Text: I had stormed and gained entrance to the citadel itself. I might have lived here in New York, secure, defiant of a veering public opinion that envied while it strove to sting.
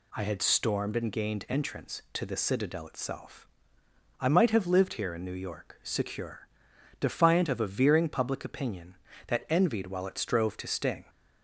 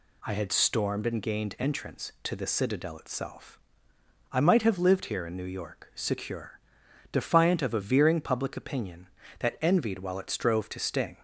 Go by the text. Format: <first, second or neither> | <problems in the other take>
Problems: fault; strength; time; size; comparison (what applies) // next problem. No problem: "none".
neither | none